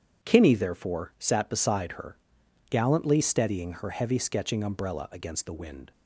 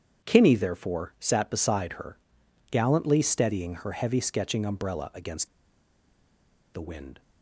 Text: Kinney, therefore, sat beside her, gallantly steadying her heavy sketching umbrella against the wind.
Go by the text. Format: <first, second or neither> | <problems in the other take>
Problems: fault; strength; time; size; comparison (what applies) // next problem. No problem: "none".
first | starts louder than the rest; strong; until 1.3 s; 8 dB; strong in the first // pauses between "against" and "the"; strong; at 5.4 s; 1.2 s long